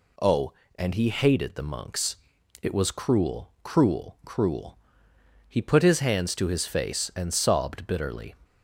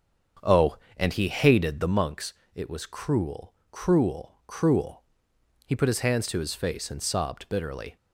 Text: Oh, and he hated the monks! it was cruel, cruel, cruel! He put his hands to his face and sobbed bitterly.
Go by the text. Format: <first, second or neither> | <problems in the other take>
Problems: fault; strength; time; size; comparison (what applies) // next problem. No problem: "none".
first | starts louder than the rest; strong; until 2.0 s; 7.5 dB